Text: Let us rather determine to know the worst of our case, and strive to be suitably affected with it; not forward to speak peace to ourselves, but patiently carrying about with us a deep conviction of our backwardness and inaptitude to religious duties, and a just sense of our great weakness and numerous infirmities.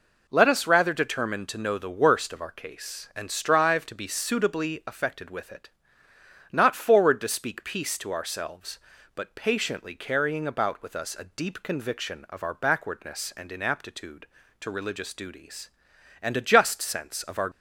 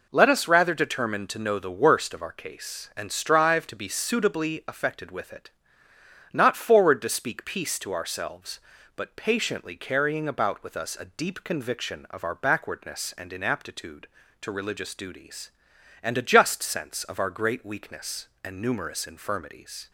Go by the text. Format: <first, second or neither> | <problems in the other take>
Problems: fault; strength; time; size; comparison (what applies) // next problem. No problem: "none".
second | stops before "great weakness and numerous infirmities"; at 17.5 s